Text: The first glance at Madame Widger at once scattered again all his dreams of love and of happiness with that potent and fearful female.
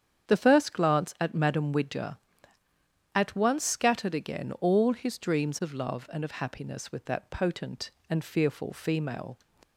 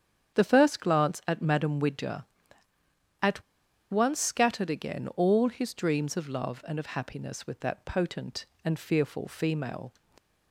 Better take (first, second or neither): first